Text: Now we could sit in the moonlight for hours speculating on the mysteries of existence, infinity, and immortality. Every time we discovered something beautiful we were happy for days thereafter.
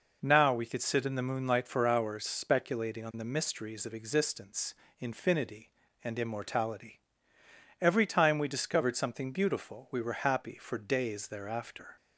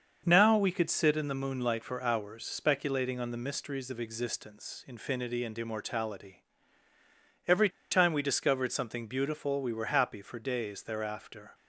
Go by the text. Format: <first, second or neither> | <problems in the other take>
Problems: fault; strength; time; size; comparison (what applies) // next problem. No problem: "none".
first | starts louder than the rest; until 1.2 s; 6.5 dB // pauses between "Every" and "time"; slight; at 7.6 s; 0.22 s long